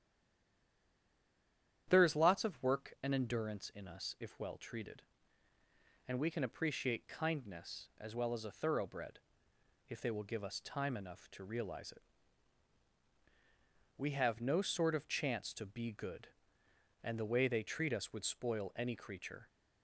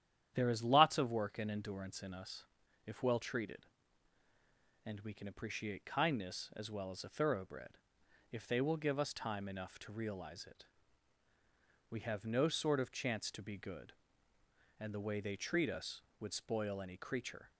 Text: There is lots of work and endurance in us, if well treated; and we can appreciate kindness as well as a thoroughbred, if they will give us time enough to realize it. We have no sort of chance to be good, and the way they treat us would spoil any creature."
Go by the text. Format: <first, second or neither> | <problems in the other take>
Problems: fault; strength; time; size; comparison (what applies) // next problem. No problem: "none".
second | stays silent before the first word; noticeable; until 1.8 s; 1.8 s long // starts louder than the rest; strong; until 2.8 s; 10 dB; strong in the second